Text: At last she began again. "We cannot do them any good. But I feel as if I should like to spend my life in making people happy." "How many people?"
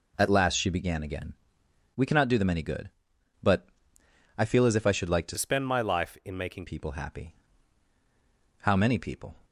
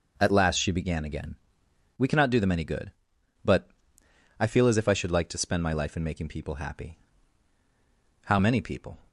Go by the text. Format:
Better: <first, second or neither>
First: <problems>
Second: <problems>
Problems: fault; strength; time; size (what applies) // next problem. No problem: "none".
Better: second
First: pauses between "But" and "I"; noticeable; at 3.6 s; 0.72 s long // changes voice from "spend" to "making"; from 5.3 to 6.6 s; 1.3 s long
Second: pauses between "But" and "I"; noticeable; at 3.6 s; 0.72 s long